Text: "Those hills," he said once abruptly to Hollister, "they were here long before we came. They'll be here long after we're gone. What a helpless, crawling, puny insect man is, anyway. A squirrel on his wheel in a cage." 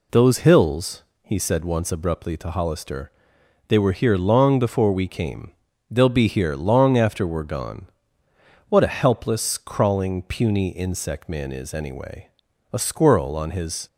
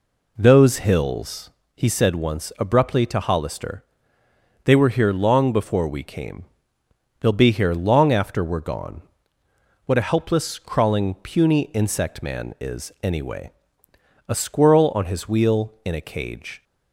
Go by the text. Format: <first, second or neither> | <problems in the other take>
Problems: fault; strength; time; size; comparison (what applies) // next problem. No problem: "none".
second | stops before "wheel in a cage"; at 13.8 s